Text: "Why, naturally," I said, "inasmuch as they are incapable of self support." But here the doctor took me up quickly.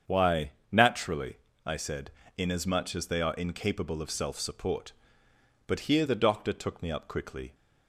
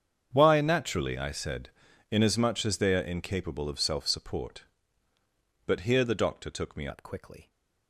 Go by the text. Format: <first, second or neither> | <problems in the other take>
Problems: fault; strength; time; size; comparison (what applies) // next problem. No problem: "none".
first | starts louder than the rest; strong; until 1.3 s; 7.5 dB; strong in the first // changes voice at "up"; from 6.9 s on; 0.5 s long